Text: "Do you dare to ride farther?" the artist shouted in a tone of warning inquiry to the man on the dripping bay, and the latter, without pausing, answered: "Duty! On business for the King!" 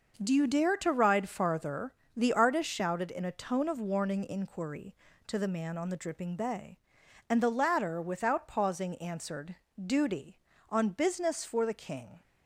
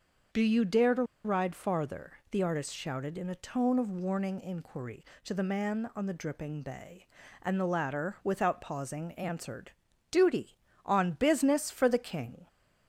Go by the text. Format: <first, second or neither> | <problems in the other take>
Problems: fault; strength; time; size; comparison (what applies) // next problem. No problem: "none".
first | starts louder than the rest; until 1.5 s; 6.5 dB // pauses between "to" and "ride"; slight; at 1.0 s; 0.21 s long